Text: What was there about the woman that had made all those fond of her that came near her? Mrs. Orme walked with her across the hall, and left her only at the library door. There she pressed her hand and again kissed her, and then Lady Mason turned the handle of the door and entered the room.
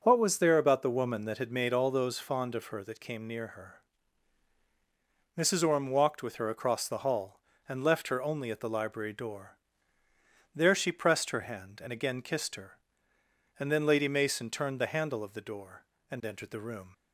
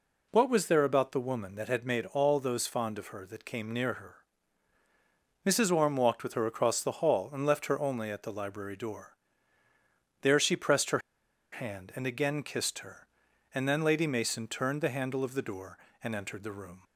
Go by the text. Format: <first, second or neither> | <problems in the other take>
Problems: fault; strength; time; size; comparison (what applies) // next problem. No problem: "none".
first | pauses between "her" and "hand"; noticeable; at 10.9 s; 0.53 s long